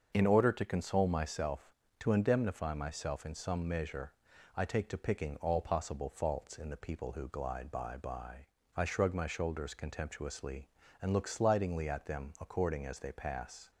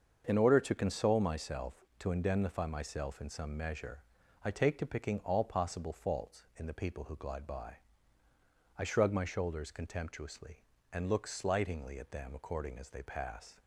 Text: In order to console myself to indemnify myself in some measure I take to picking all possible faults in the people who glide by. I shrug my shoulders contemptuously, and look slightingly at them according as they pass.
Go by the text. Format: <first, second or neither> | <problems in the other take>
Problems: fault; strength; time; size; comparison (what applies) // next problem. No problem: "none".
second | starts louder than the rest; until 1.1 s; 6.5 dB; also in the second // pauses between "measure" and "I"; at 4.1 s; 0.42 s long; also in the second // says "by" twice; at 7.9 s